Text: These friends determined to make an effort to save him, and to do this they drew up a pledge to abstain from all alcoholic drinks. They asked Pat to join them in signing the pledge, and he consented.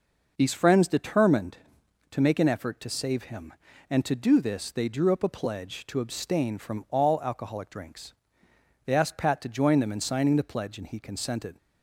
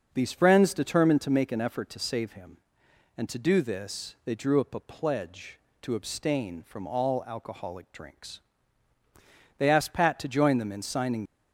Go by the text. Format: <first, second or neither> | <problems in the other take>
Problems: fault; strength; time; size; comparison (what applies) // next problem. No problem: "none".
first | starts louder than the rest; until 1.1 s; 6.5 dB // stops before "the pledge and he consented"; at 11.2 s